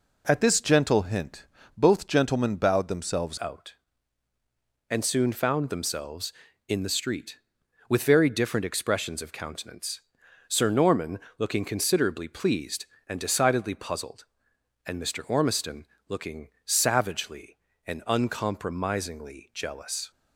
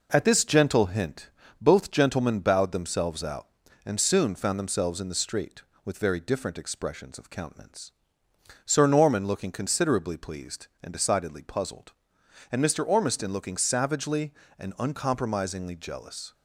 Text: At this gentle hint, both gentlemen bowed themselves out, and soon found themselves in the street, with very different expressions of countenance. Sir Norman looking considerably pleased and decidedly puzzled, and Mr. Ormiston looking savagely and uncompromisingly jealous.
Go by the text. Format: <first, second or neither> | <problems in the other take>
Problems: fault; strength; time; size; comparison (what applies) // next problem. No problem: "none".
second | changes voice at "out"; from 3.4 s on; 16.7 s long // pauses between "Norman" and "looking"; slight; at 11.1 s; 0.20 s long // pauses between "Ormiston" and "looking"; slight; at 15.8 s; 0.22 s long // pauses between "looking" and "savagely"; slight; at 16.4 s; 0.18 s long